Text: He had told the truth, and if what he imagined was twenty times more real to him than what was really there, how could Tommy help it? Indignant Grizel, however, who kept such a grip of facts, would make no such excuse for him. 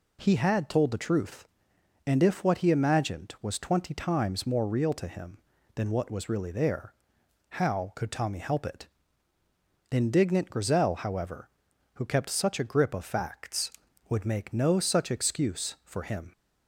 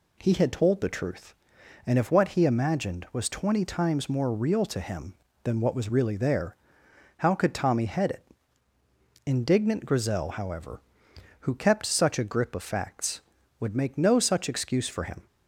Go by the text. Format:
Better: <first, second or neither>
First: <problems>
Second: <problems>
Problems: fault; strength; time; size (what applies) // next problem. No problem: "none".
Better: first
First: none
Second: says "head" for "help"; at 7.8 s